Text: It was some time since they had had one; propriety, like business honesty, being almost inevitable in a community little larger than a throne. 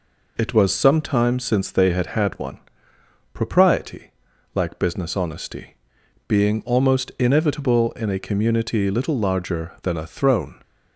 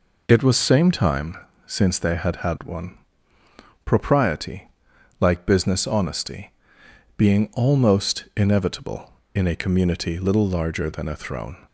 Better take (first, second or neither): first